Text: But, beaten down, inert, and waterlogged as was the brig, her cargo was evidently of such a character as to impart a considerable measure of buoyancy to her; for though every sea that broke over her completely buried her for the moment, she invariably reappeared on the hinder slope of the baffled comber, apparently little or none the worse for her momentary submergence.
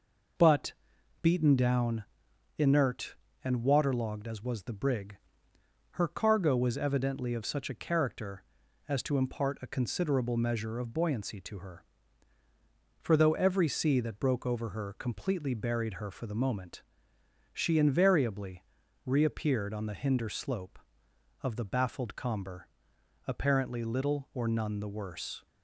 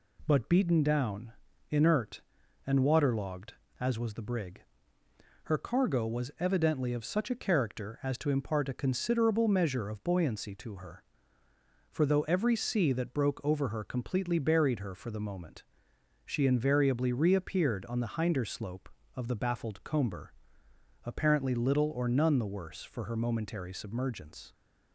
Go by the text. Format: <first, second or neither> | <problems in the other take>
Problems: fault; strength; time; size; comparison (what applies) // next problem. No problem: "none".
second | pauses between "invariably" and "reappeared"; at 18.6 s; 0.44 s long // stops before "for her momentary submergence"; at 25.4 s